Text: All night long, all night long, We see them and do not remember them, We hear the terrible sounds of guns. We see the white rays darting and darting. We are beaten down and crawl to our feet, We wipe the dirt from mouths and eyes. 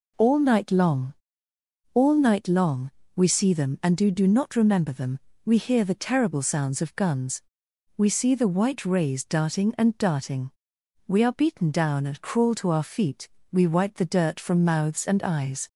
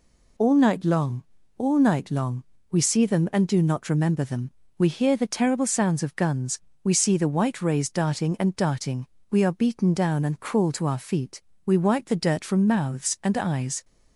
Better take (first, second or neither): second